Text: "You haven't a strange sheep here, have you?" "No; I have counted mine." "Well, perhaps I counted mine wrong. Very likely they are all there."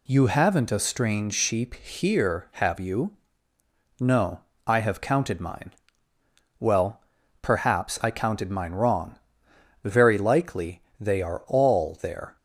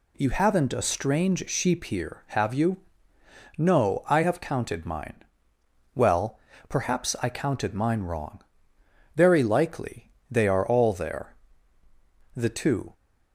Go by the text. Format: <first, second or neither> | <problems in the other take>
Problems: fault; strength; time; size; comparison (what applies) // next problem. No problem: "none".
first | pauses between "likely" and "they"; slight; at 10.1 s; 0.18 s long; slight in the first // goes on to say "The two"; from 12.3 s on; 0.56 s long